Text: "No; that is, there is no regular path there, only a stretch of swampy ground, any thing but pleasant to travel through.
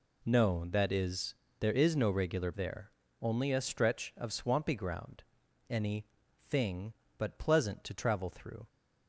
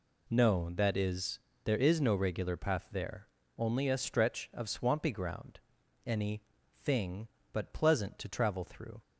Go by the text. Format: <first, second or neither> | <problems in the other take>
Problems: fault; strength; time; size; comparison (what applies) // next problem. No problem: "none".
second | skips "path"; at 2.5 s // pauses between "any" and "thing"; at 6.0 s; 0.42 s long; also in the second